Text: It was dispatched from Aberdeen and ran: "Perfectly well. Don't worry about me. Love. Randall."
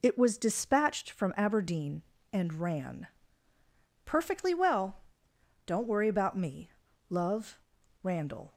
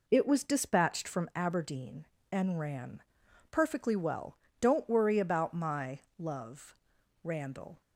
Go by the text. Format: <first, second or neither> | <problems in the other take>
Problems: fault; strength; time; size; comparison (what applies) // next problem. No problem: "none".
first | says "my" for "me"; at 5.5 s